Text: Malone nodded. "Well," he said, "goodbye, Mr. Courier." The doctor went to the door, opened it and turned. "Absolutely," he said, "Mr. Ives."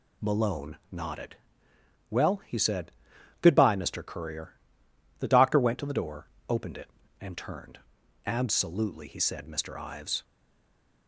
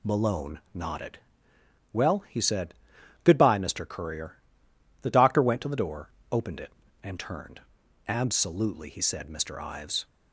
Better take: second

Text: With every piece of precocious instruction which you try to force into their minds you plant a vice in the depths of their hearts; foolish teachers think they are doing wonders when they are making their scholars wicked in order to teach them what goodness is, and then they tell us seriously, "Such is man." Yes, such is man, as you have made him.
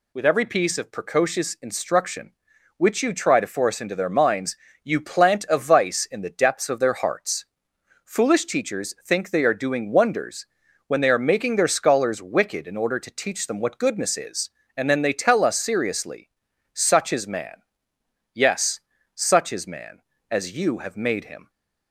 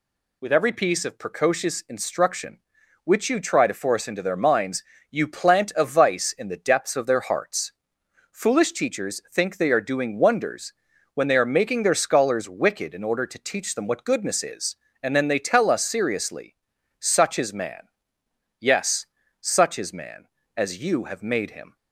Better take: neither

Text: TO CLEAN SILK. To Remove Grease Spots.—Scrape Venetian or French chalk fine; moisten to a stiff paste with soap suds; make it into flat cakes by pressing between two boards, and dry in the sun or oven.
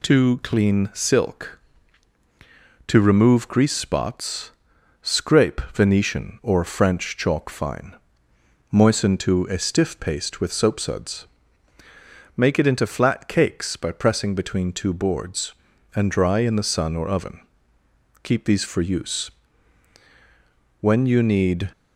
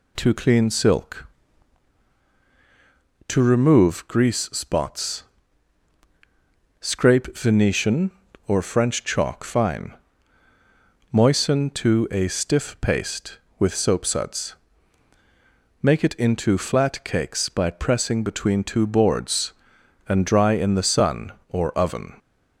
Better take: second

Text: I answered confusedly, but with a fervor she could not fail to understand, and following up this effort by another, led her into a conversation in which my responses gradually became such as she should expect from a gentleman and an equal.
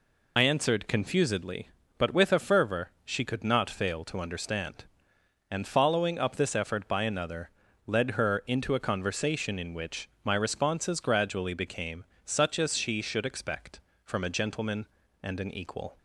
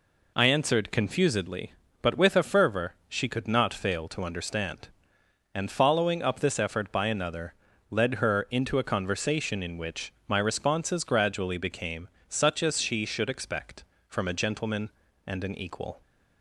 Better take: second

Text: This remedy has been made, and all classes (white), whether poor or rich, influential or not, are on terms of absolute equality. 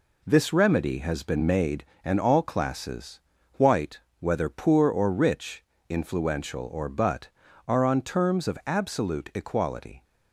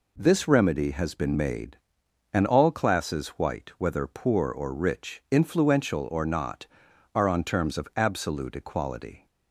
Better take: second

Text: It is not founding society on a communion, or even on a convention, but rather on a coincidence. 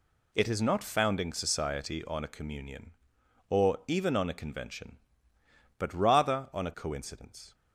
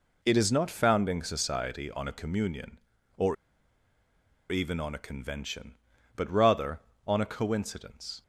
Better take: first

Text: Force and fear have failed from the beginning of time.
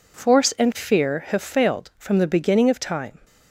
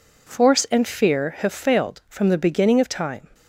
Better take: neither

